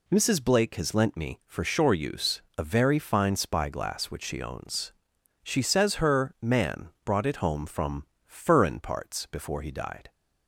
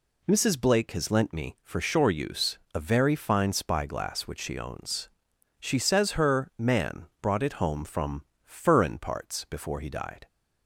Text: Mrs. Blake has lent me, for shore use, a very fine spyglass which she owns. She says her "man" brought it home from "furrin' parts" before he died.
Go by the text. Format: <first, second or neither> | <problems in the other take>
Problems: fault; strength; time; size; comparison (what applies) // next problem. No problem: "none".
neither | pauses between "from" and "furrin"; slight; the same in both